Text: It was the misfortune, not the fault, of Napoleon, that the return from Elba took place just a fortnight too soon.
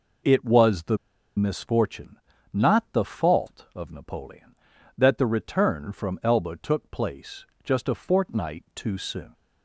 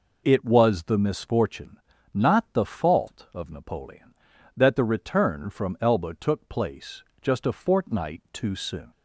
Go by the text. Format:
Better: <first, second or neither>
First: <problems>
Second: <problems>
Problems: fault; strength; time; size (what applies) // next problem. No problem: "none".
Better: second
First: pauses between "the" and "misfortune"; at 0.9 s; 0.39 s long // pauses between "place" and "just"; slight; at 7.4 s; 0.20 s long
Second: pauses between "place" and "just"; slight; at 7.0 s; 0.20 s long